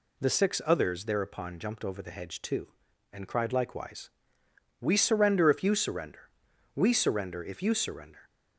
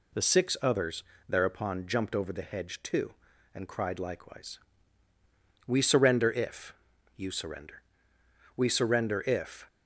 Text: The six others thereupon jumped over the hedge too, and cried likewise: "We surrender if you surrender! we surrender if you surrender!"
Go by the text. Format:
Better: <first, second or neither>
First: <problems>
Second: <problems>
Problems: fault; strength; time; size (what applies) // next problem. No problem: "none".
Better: first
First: none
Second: pauses between "others" and "thereupon"; slight; at 1.0 s; 0.26 s long // pauses between "if" and "you"; at 6.7 s; 0.44 s long // stops before "you surrender"; at 9.6 s